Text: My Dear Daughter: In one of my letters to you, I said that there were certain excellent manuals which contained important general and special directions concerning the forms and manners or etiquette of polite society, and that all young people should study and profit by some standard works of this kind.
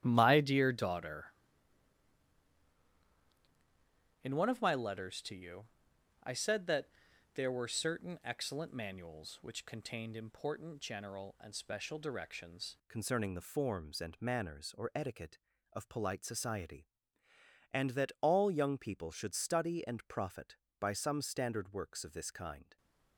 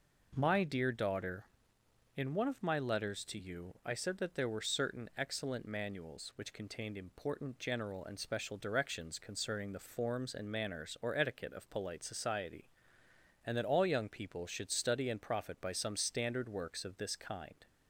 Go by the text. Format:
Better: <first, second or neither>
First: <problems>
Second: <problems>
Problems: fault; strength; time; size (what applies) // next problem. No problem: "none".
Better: second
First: starts louder than the rest; strong; until 1.0 s; 11.5 dB // pauses between "that" and "there"; noticeable; at 6.8 s; 0.46 s long // changes voice at "concerning"; from 12.8 s on; 9.9 s long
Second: none